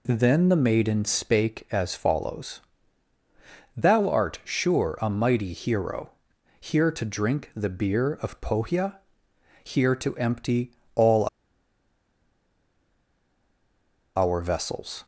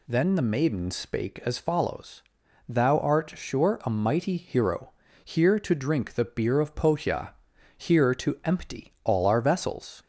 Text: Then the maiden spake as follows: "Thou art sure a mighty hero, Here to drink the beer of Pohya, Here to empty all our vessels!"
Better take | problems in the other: second | pauses between "empty" and "all"; slight; at 10.7 s; 0.24 s long // pauses between "all" and "our"; strong; at 11.2 s; 2.8 s long

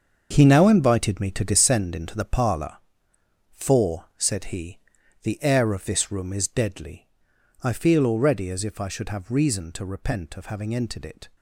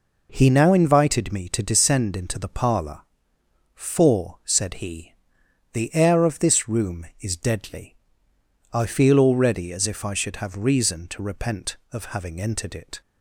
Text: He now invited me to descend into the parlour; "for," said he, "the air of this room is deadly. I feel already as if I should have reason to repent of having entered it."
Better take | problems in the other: second | gets quieter; strong; throughout; 11.5 dB

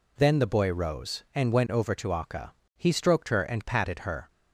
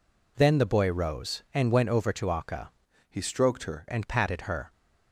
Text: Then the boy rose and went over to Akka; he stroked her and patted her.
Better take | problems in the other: first | changes voice from "he" to "her"; from 3.0 to 3.8 s; 0.8 s long

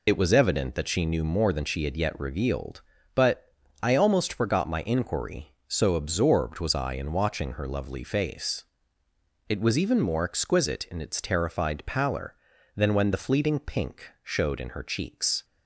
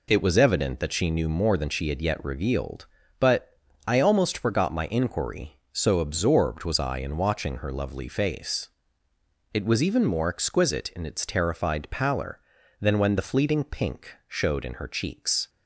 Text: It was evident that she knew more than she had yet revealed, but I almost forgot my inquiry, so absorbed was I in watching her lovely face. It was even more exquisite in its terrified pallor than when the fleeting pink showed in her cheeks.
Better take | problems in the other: second | loses the start of "It"; at 0.0 s; 40 ms // pauses between "but" and "I"; slight; at 3.5 s; 0.32 s long; slight in the second

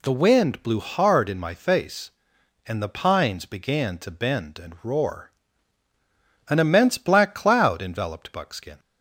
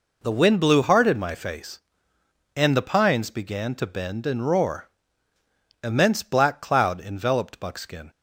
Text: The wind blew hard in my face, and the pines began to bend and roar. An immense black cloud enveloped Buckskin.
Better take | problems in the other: first | skips "An"; at 5.3 s

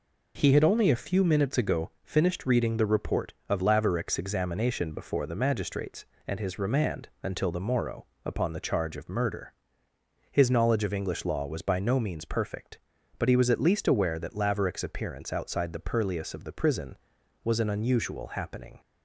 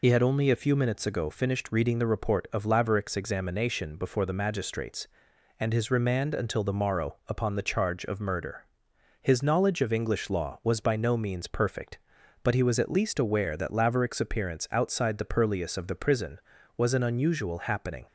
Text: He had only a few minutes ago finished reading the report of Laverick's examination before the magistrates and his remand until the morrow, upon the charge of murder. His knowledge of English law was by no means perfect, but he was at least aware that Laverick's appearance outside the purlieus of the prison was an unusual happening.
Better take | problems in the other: first | loses the start of "He"; at 0.0 s; 60 ms

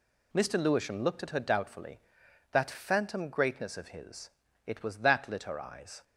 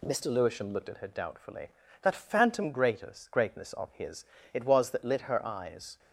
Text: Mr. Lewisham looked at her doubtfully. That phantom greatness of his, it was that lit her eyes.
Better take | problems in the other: first | says "greatness" twice; at 3.3 s

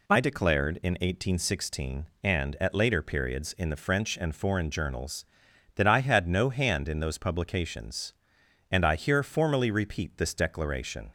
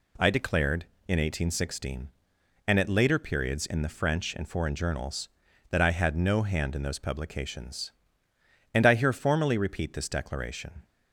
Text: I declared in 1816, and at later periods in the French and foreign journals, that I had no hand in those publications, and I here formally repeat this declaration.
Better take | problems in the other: neither | none

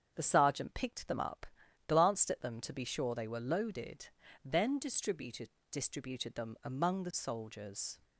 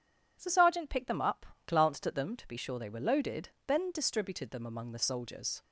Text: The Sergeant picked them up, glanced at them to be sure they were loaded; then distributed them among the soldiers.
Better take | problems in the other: second | starts louder than the rest; strong; until 1.1 s; 7.5 dB // says "distributed" twice; at 5.7 s

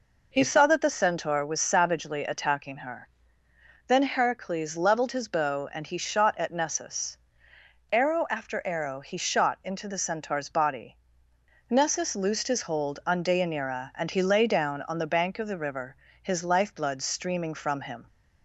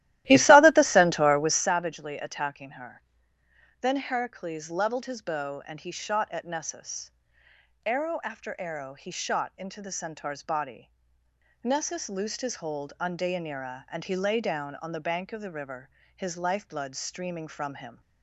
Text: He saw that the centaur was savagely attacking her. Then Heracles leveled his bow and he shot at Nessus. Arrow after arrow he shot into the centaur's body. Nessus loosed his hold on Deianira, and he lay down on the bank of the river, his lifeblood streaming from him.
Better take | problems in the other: first | starts louder than the rest; strong; until 1.8 s; 15 dB

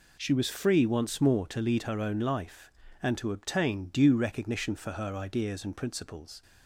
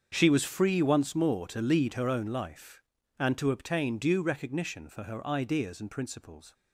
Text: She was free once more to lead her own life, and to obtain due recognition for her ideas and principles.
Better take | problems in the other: first | gets quieter; strong; throughout; 15 dB

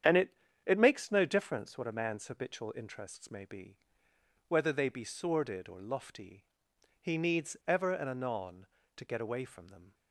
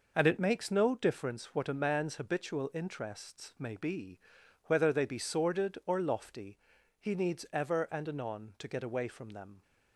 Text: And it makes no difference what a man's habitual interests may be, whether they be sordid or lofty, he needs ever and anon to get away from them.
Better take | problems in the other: second | starts louder than the rest; strong; until 1.3 s; 9 dB // says "it" twice; at 0.6 s

